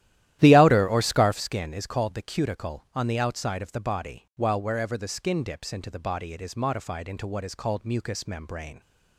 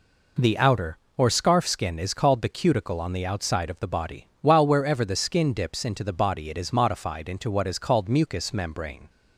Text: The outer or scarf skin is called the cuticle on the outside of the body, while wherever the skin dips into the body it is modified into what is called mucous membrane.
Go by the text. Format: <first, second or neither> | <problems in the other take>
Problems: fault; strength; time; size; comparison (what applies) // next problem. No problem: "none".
second | starts louder than the rest; strong; until 1.5 s; 13 dB